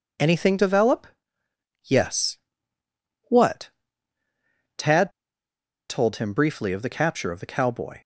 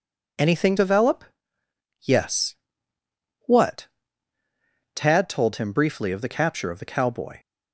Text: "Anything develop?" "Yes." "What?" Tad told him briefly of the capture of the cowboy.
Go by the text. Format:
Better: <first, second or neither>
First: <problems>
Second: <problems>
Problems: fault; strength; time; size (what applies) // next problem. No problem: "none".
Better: second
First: pauses between "Tad" and "told"; noticeable; at 5.1 s; 0.78 s long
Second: none